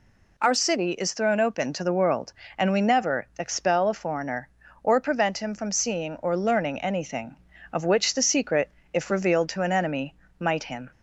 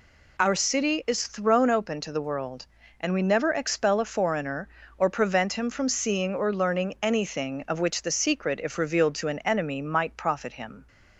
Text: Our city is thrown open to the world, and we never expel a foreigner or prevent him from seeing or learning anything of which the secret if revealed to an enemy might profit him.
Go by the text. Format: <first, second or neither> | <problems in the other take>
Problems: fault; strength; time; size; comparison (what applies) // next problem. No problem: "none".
second | pauses between "secret" and "if"; slight; at 8.6 s; 0.24 s long // pauses between "enemy" and "might"; slight; at 10.1 s; 0.24 s long // skips "profit"; at 10.6 s